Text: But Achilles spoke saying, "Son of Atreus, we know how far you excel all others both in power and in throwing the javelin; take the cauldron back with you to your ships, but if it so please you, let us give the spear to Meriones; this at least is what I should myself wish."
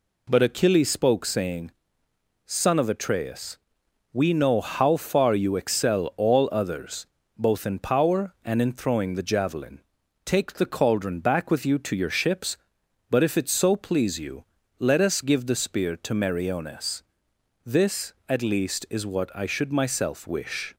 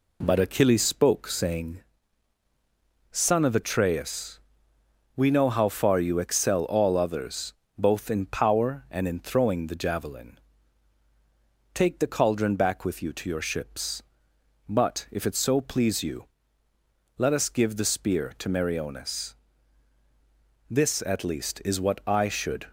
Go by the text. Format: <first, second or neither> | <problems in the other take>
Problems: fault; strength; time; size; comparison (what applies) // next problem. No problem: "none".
first | pauses between "others" and "both"; slight; at 7.5 s; 0.22 s long; slight in the first // stops before "myself wish"; at 22.6 s